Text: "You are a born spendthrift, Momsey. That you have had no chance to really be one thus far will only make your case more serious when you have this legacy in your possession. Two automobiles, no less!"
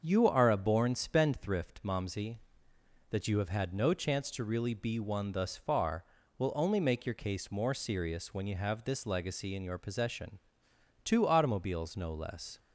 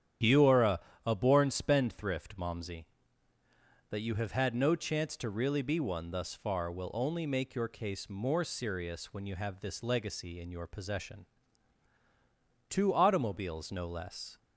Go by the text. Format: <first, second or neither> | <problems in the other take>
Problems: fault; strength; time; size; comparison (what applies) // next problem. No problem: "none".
first | starts louder than the rest; strong; until 1.4 s; 9.5 dB; also in the first // says "a" twice; at 1.0 s